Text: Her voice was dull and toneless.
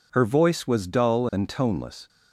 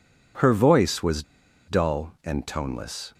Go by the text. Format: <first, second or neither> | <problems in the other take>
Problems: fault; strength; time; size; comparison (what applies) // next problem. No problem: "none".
first | pauses between "was" and "dull"; noticeable; at 1.2 s; 0.46 s long